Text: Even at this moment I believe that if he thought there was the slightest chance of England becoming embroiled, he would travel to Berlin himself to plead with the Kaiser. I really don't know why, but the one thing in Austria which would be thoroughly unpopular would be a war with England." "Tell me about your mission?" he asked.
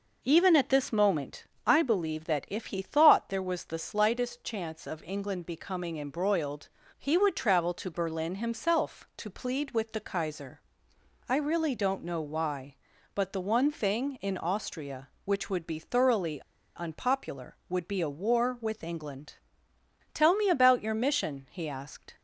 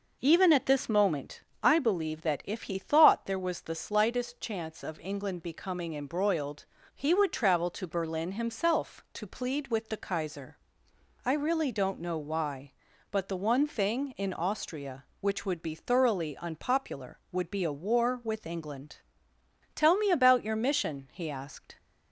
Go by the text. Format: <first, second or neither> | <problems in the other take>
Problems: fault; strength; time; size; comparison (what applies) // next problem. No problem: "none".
second | pauses between "moment" and "I"; slight; at 1.4 s; 0.22 s long; slight in the second // pauses between "thoroughly" and "unpopular"; slight; at 16.4 s; 0.35 s long